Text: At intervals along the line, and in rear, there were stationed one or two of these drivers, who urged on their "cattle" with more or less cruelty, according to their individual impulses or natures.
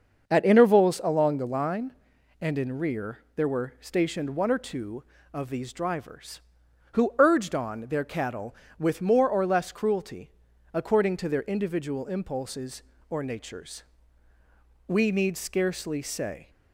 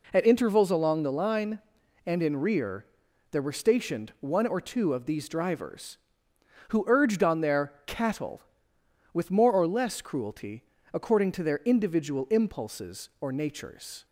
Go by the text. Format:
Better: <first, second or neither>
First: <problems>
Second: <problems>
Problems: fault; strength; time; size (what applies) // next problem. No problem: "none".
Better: second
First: starts louder than the rest; until 1.3 s; 6.5 dB // goes on to say "We need scarcely say"; from 14.8 s on; 1.6 s long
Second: none